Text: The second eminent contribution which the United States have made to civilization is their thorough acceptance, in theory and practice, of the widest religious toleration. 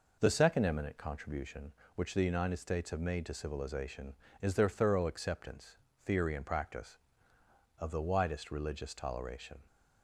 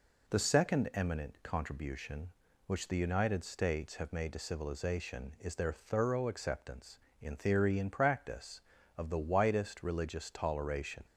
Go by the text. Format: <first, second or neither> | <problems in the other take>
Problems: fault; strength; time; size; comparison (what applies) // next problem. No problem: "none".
second | skips "in"; at 5.9 s